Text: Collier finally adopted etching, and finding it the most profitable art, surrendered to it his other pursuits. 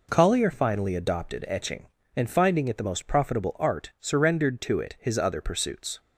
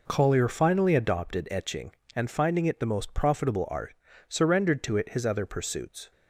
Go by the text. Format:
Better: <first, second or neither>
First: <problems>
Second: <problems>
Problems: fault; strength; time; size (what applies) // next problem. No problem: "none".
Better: neither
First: none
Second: none